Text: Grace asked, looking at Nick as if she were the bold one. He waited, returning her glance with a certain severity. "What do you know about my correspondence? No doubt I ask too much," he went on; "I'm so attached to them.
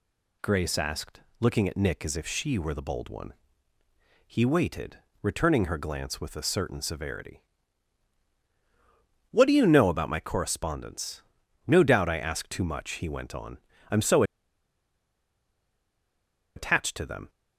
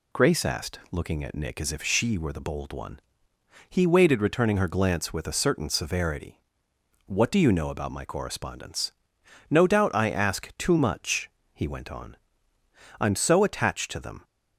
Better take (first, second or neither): second